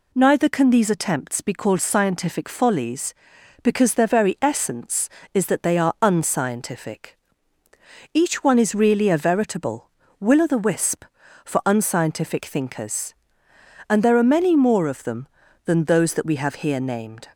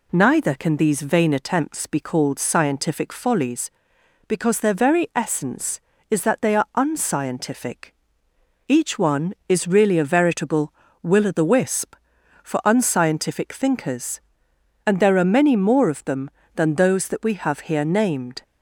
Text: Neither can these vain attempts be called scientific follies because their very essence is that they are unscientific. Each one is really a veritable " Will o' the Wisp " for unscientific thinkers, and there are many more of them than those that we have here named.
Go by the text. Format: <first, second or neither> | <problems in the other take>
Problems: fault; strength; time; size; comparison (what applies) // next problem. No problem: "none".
second | skips "vain"; at 0.9 s